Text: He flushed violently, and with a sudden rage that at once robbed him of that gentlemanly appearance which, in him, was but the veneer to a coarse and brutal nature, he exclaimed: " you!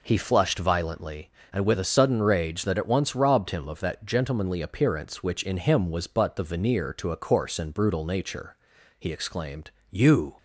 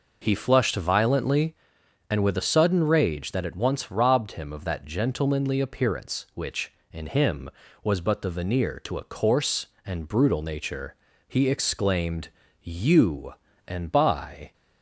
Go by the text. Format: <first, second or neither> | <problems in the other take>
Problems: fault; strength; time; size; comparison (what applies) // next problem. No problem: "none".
first | goes on to say "and by"; noticeable; from 13.6 s on; 0.86 s long